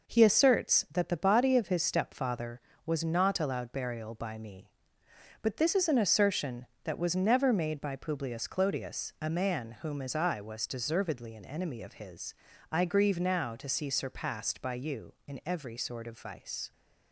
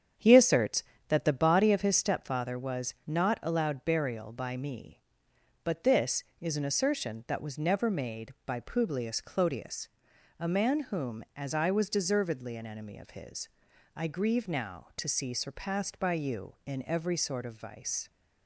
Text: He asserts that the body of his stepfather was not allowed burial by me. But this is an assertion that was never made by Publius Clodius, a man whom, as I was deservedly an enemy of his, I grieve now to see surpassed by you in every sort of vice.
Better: first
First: none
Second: starts louder than the rest; strong; until 2.0 s; 8 dB

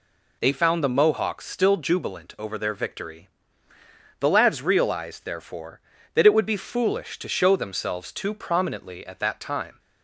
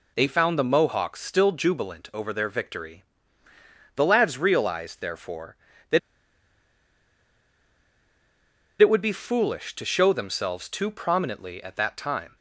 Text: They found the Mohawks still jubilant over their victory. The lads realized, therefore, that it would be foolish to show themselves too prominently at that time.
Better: first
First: none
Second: pauses between "that" and "it"; strong; at 5.9 s; 2.8 s long

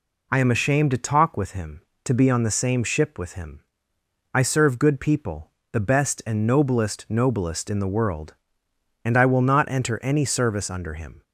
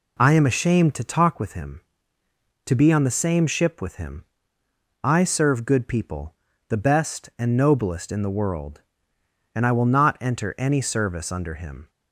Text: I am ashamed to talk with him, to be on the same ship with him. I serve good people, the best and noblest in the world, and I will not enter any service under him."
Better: second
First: says "noblest" twice; at 7.0 s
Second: none

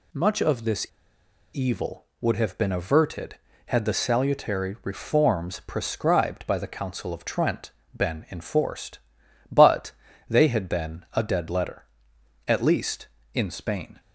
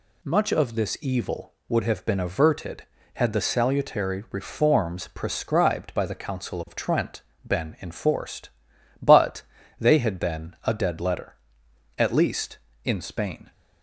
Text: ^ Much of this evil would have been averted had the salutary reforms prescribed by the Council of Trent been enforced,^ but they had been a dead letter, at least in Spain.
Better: second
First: pauses between "this" and "evil"; noticeable; at 0.8 s; 0.67 s long // pauses between "Trent" and "been"; slight; at 7.6 s; 0.26 s long // pauses between "but" and "they"; slight; at 9.9 s; 0.36 s long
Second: pauses between "Trent" and "been"; slight; at 7.2 s; 0.26 s long // pauses between "but" and "they"; slight; at 9.4 s; 0.36 s long

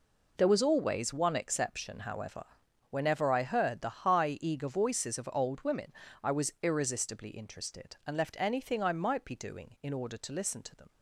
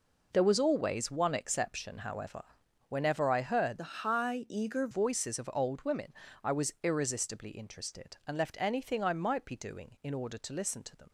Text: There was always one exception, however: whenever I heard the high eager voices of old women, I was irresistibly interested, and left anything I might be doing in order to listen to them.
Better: first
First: none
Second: changes voice from "the" to "eager"; from 3.7 to 4.8 s; 1.1 s long

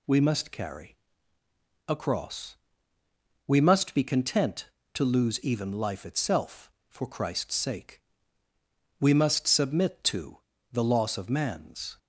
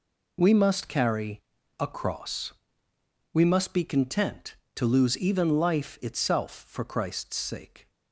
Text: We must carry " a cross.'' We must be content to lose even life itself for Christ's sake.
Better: second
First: goes on to say "We must submit to the loss of man's"; strong; from 9.0 s on; 2.9 s long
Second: none

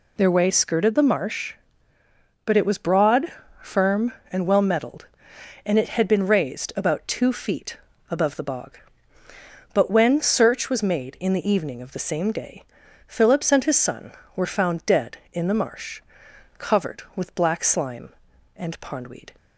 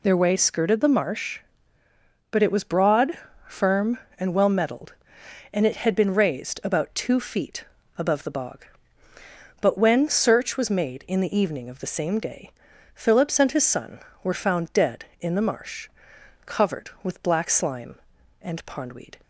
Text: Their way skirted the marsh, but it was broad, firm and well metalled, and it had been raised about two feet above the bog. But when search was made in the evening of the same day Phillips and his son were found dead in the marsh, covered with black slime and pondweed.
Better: neither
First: pauses between "feet" and "above"; slight; at 7.7 s; 0.34 s long // pauses between "day" and "Phillips"; at 12.6 s; 0.42 s long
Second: pauses between "feet" and "above"; slight; at 7.6 s; 0.34 s long // pauses between "day" and "Phillips"; at 12.5 s; 0.42 s long

